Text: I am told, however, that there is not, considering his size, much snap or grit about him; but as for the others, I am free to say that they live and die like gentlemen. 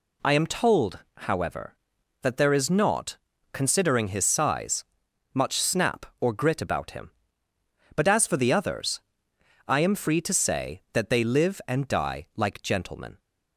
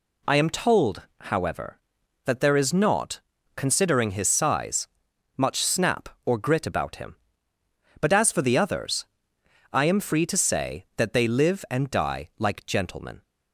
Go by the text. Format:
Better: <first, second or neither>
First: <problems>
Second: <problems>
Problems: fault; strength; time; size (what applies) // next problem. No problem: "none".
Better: neither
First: none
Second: none